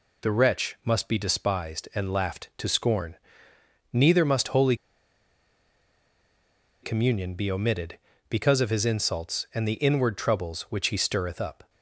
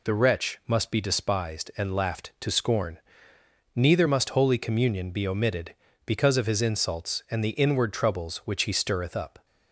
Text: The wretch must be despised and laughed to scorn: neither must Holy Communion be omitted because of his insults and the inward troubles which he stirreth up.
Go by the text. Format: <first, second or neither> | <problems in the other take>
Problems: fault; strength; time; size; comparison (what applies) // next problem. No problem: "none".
second | pauses between "Holy" and "Communion"; strong; at 4.7 s; 2.0 s long